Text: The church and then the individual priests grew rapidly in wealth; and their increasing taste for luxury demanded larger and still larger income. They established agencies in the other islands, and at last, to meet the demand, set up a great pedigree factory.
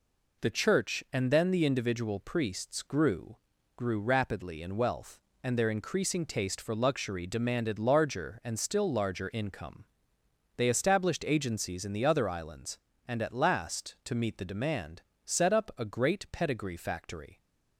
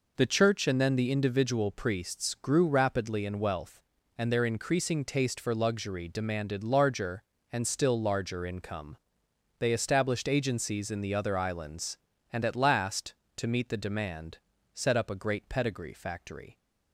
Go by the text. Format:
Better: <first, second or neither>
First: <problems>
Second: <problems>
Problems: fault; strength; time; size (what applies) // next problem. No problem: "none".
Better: second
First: says "grew" twice; at 3.7 s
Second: none